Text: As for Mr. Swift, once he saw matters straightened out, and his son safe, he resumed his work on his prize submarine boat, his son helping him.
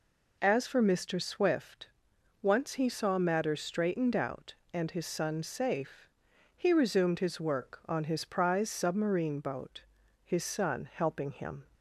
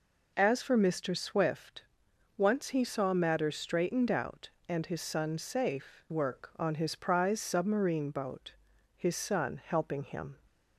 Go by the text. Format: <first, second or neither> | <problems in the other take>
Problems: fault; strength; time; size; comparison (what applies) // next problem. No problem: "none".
first | skips "he resumed his"; at 6.0 s